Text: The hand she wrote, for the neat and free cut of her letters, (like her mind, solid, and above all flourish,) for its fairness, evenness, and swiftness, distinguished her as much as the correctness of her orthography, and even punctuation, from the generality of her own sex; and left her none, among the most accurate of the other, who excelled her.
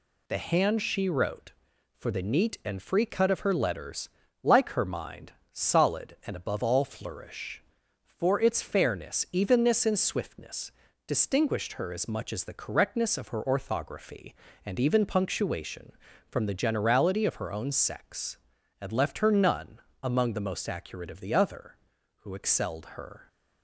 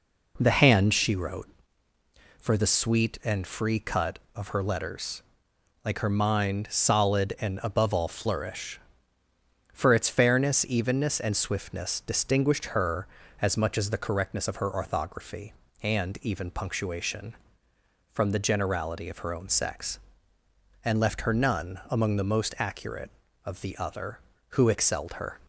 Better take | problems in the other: first | says "sweet" for "neat"; at 2.6 s

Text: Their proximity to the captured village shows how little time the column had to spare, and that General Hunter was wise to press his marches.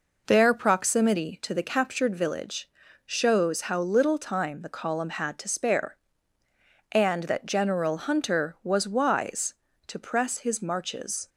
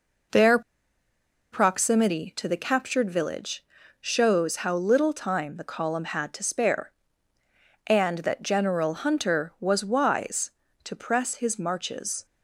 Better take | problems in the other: first | pauses between "Their" and "proximity"; noticeable; at 0.5 s; 0.92 s long // pauses between "village" and "shows"; slight; at 3.6 s; 0.34 s long; slight in the first

